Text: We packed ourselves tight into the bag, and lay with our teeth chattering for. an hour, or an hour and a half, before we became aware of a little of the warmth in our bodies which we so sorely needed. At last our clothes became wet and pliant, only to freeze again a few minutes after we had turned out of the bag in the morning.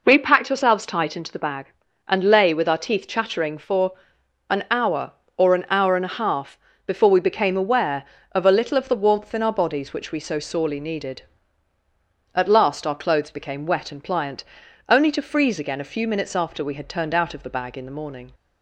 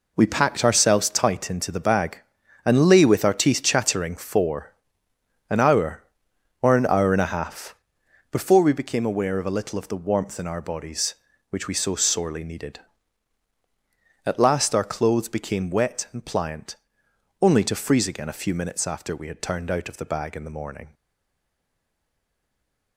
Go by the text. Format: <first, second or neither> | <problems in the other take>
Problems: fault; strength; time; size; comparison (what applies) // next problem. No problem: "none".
first | stays silent after the last word; noticeable; from 20.9 s on; 2.0 s long